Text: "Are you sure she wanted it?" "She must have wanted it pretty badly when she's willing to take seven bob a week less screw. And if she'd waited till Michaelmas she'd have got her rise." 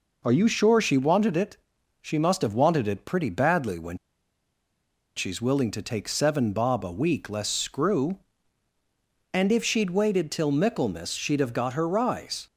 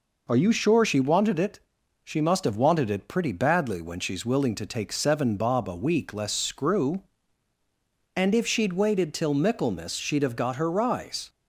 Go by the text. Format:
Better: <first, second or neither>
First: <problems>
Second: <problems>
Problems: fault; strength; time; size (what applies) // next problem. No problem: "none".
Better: second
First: pauses between "when" and "she's"; at 3.9 s; 1.1 s long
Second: none